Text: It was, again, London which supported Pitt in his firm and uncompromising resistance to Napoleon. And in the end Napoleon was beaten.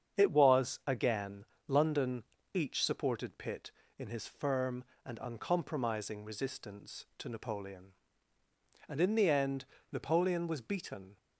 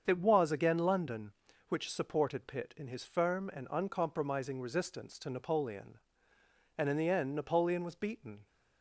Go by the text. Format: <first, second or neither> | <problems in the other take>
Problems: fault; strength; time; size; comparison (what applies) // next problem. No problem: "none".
second | starts louder than the rest; strong; until 1.2 s; 7.5 dB; strong in the second // says "each" for "which"; at 2.5 s // pauses between "end" and "Napoleon"; slight; at 9.6 s; 0.26 s long